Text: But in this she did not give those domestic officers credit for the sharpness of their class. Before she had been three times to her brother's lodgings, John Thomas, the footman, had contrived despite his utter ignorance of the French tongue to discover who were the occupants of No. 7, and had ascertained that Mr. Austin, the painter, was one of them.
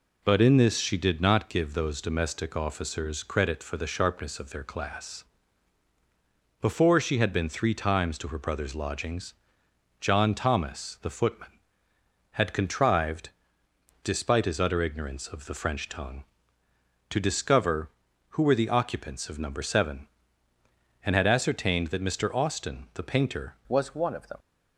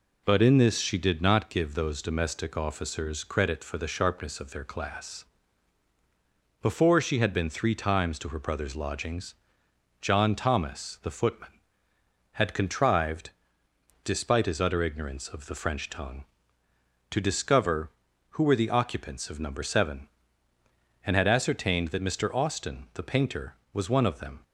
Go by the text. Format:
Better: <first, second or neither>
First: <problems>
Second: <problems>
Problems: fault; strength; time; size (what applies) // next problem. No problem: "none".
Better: second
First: pauses between "contrived" and "despite"; noticeable; at 13.3 s; 0.74 s long // changes voice at "was"; from 23.6 s on; 0.7 s long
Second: pauses between "contrived" and "despite"; noticeable; at 13.3 s; 0.74 s long